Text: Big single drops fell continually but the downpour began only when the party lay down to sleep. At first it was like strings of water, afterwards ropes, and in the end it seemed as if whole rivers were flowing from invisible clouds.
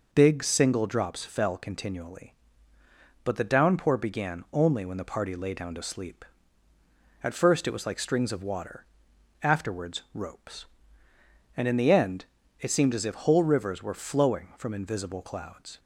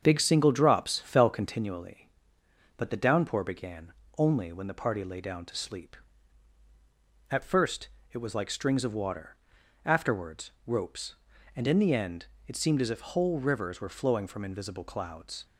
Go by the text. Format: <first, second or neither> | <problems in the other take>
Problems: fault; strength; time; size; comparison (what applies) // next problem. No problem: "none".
first | starts louder than the rest; strong; until 1.6 s; 7.5 dB // pauses between "began" and "only"; slight; at 3.9 s; 0.24 s long // pauses between "first" and "it"; slight; at 7.8 s; 0.24 s long // pauses between "afterwards" and "ropes"; slight; at 10.5 s; 0.16 s long // pauses between "end" and "it"; slight; at 12.2 s; 0.24 s long; slight in the first